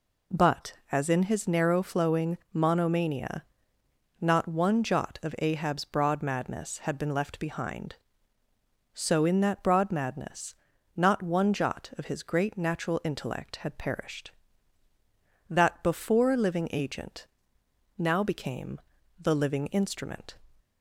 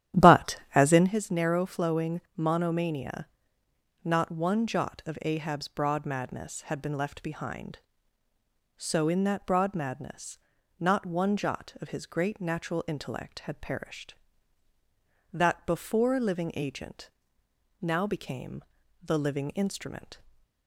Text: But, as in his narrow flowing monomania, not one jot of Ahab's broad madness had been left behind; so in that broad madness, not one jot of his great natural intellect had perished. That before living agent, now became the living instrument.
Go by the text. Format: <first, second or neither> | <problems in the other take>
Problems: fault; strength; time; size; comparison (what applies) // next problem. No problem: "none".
first | starts louder than the rest; strong; until 1.1 s; 12 dB // pauses between "flowing" and "monomania"; slight; at 2.2 s; 0.16 s long; slight in the first // pauses between "became" and "the"; at 18.6 s; 0.40 s long; also in the first // stays silent after the last word; slight; from 20.1 s on; 0.5 s long